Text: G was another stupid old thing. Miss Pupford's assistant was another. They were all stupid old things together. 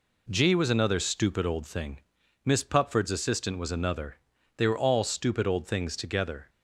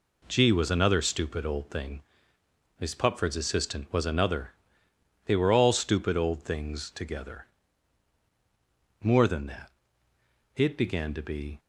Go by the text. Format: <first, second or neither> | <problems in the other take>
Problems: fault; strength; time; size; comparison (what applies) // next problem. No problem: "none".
first | goes on to say "More than that it began to be"; strong; from 9.0 s on; 2.5 s long